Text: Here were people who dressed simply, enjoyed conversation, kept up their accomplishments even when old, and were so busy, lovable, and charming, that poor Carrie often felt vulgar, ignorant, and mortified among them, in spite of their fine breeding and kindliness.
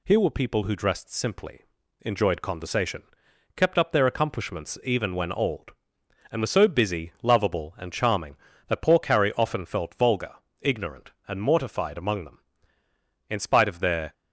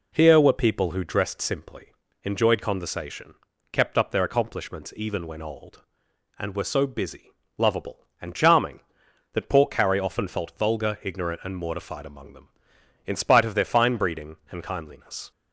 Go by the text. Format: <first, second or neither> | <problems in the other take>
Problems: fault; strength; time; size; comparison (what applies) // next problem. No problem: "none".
second | stops before "fine breeding and kindliness"; at 14.1 s